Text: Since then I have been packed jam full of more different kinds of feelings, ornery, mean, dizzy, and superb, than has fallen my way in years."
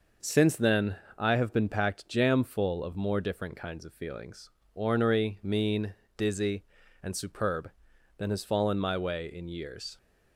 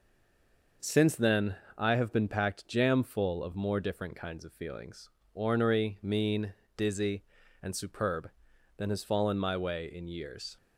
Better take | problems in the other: first | stays silent before the first word; slight; until 0.8 s; 0.8 s long // pauses between "then" and "I"; slight; at 1.5 s; 0.20 s long; slight in the first

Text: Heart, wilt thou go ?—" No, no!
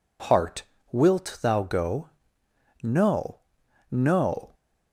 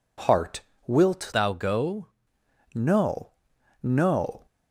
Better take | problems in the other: first | changes voice from "thou" to "go"; from 1.3 to 2.0 s; 0.7 s long

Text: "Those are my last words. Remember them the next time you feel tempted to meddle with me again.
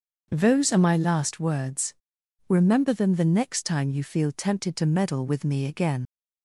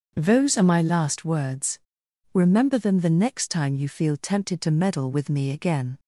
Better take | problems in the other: second | starts louder than the rest; until 1.3 s; 6.5 dB; also in the second // leaves "again" unfinished; at 6.0 s; 90 ms

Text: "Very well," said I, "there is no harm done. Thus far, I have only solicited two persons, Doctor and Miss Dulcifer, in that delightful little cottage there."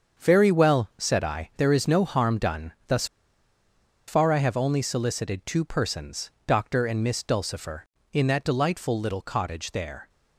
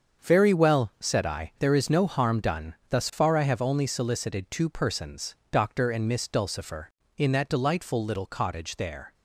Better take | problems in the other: second | starts louder than the rest; until 1.2 s; 7 dB; also in the second // pauses between "Thus" and "far"; at 3.0 s; 1.0 s long

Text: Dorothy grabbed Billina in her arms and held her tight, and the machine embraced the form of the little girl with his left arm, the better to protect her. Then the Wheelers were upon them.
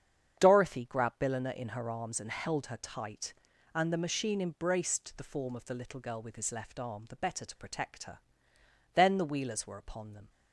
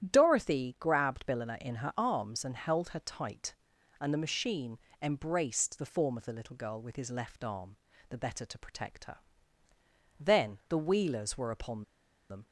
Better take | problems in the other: first | starts louder than the rest; strong; until 1.1 s; 11 dB; strong in the first // pauses between "machine" and "embraced"; slight; at 4.7 s; 0.20 s long // pauses between "upon" and "them"; noticeable; at 11.8 s; 0.46 s long

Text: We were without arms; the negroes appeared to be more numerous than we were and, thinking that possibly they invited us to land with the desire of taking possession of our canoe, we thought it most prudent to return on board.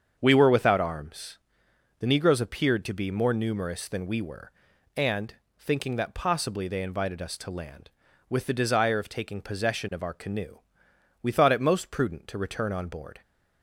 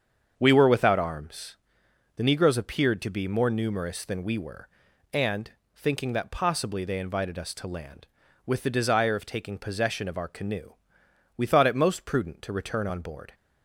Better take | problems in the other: neither | starts louder than the rest; strong; the same in both

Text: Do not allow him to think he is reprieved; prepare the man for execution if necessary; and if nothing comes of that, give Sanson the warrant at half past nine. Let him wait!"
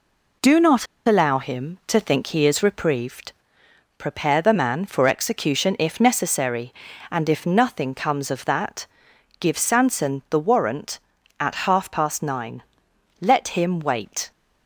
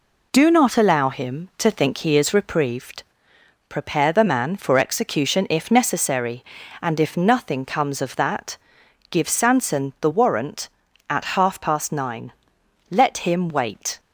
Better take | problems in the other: second | pauses between "not" and "allow"; slight; at 0.8 s; 0.20 s long

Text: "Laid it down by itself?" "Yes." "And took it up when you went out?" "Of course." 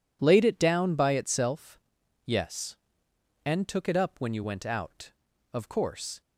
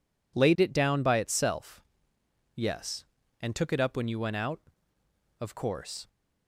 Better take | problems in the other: neither | none

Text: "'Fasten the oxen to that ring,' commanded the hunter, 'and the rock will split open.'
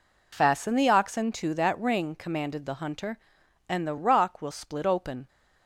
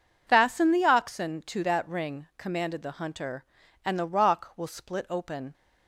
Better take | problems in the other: neither | none

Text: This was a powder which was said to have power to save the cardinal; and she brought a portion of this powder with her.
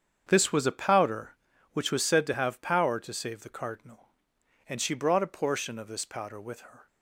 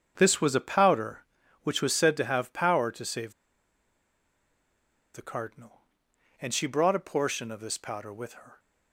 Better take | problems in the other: first | starts louder than the rest; strong; until 1.1 s; 7.5 dB; strong in the first // pauses between "save" and "the"; strong; at 3.3 s; 1.8 s long

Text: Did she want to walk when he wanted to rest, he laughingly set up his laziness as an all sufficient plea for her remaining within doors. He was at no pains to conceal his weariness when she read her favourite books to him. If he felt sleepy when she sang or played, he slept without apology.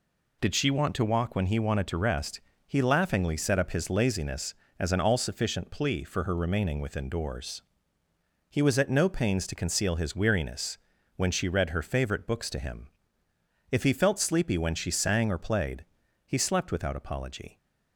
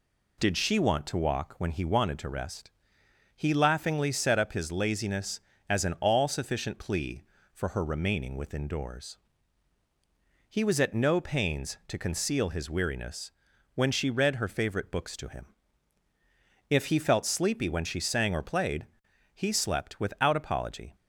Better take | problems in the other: neither | pauses between "weariness" and "when"; the same in both

